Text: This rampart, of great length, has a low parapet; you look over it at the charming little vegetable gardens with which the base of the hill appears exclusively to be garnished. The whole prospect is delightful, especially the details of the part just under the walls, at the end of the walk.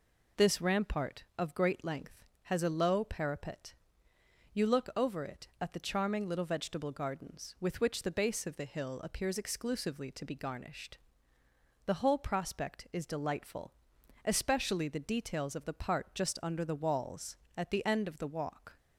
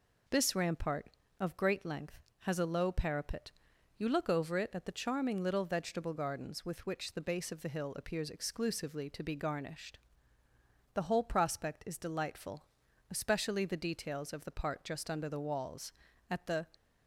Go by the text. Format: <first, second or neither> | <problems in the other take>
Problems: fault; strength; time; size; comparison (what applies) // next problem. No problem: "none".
first | stops before "end of the walk"; at 16.7 s